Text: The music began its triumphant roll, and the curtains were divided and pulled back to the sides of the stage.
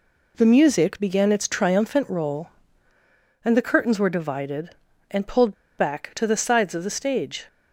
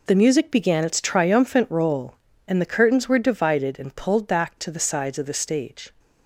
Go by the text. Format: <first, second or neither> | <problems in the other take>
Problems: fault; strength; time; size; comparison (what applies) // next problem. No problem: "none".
second | pauses between "pulled" and "back"; slight; at 5.5 s; 0.24 s long